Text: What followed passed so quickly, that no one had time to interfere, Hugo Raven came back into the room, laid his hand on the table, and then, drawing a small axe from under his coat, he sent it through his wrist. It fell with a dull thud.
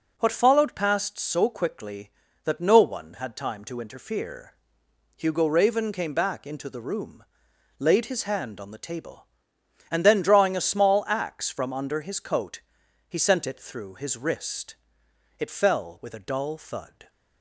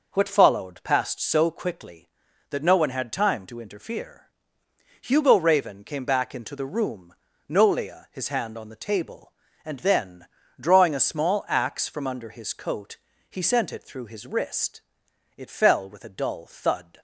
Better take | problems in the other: first | says "nolia" for "laid"; at 7.4 s

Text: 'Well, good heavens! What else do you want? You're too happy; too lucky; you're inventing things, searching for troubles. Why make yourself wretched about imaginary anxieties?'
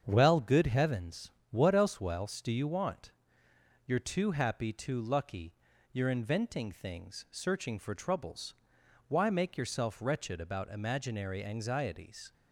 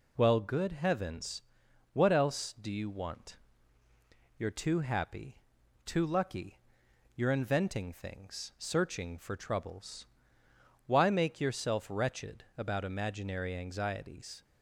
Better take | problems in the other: second | starts louder than the rest; strong; until 1.0 s; 7.5 dB // says "else" twice; at 2.0 s

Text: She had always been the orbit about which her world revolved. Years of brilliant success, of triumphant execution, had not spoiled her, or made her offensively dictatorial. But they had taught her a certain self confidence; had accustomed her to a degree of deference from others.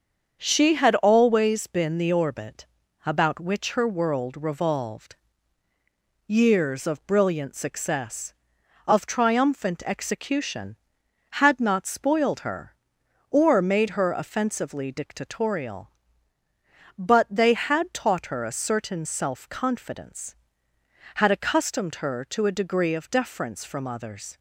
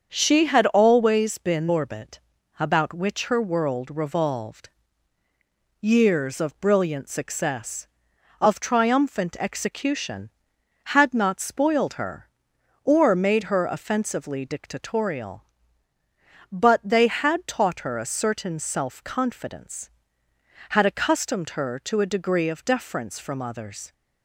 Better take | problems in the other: first | starts louder than the rest; until 1.1 s; 6.5 dB; also in the first // skips "the"; at 1.6 s // pauses between "orbit" and "about"; at 2.1 s; 0.40 s long; also in the first

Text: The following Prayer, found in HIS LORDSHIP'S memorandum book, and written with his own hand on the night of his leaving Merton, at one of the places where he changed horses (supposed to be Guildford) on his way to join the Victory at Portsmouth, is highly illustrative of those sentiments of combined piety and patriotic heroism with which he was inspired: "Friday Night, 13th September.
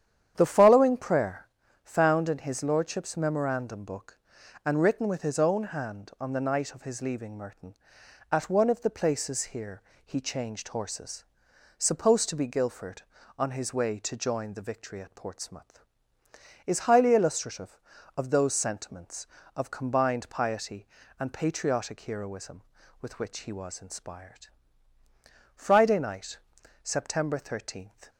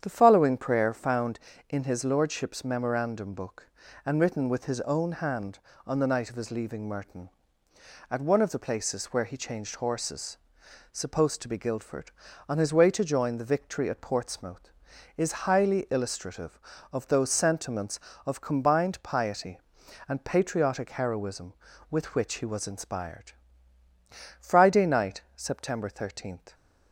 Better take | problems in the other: second | starts louder than the rest; strong; until 1.3 s; 9.5 dB; strong in the second // says "here" for "where"; at 9.5 s

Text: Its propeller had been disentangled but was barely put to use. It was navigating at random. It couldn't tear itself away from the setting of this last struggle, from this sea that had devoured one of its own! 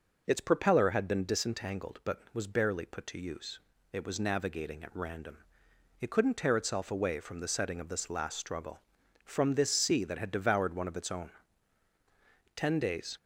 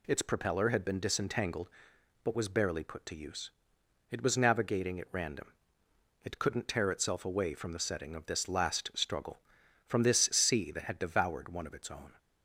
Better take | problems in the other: second | goes on to say "Ten days"; noticeable; from 12.5 s on; 0.62 s long

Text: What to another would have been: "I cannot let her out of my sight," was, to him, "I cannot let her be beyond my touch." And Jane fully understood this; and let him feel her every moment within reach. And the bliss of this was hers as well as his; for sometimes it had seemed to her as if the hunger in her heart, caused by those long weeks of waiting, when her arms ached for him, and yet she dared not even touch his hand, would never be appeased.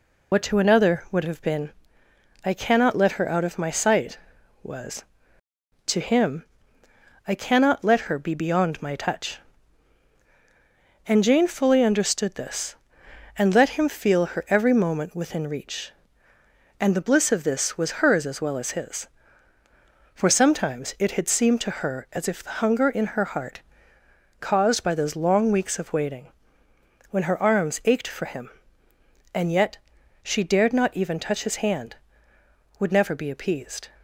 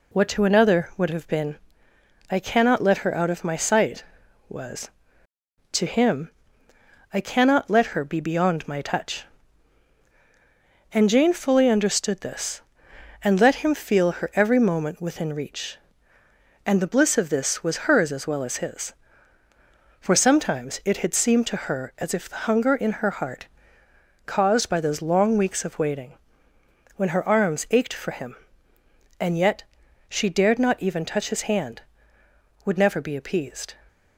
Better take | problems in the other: second | loses the start of "What"; at 0.3 s; 65 ms // pauses between "yet" and "she"; at 29.7 s; 0.44 s long; also in the second

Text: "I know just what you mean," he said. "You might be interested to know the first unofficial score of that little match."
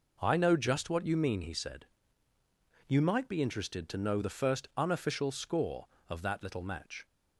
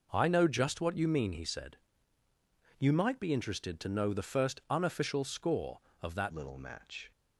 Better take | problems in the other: first | changes voice at "little"; from 6.3 s on; 0.8 s long

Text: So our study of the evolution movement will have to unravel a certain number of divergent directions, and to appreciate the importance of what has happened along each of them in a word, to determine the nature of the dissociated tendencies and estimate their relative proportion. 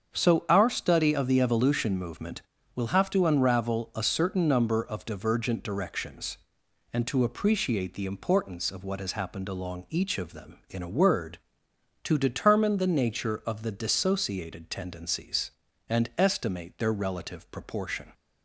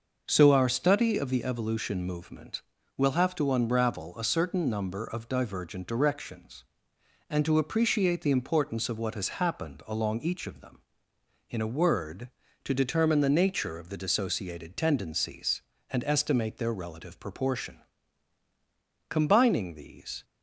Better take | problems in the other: first | starts louder than the rest; noticeable; until 1.2 s; 6 dB; strong in the first // goes on to say "Combining these"; noticeable; from 19.0 s on; 1.1 s long

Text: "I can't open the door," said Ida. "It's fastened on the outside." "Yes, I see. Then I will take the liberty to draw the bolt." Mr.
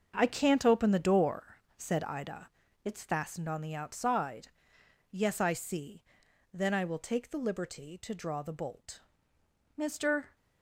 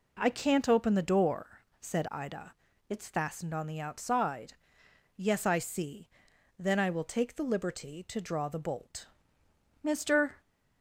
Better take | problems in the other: second | gets quieter; strong; throughout; 11 dB

